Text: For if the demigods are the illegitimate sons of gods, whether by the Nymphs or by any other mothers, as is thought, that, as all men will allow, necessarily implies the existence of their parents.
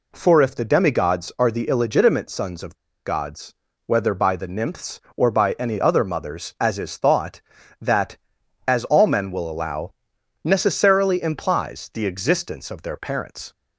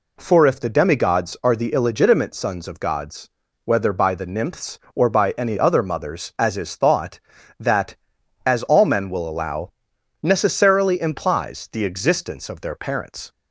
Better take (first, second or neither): second